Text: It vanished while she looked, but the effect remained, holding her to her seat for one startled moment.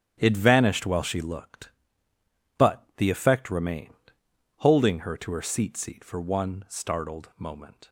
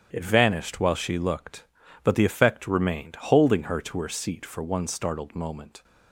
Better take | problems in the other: second | starts louder than the rest; strong; until 1.1 s; 10 dB; strong in the second // says "seat" twice; at 5.7 s

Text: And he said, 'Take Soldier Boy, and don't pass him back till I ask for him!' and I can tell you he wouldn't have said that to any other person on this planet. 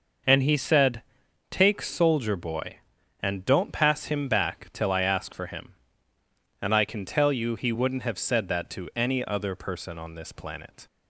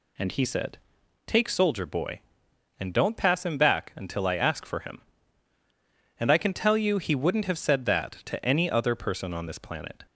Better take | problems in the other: first | says "until" for "till"; at 3.9 s

